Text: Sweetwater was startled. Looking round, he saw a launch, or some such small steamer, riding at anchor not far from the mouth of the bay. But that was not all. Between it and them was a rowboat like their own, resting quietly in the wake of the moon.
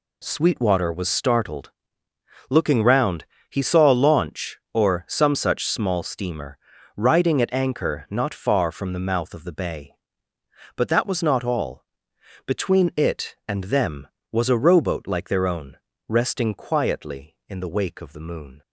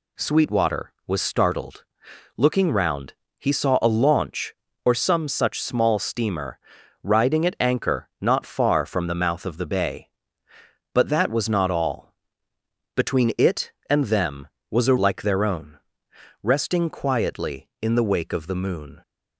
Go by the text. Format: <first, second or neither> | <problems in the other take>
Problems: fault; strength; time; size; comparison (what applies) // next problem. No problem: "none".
first | skips "rowboat"; at 14.9 s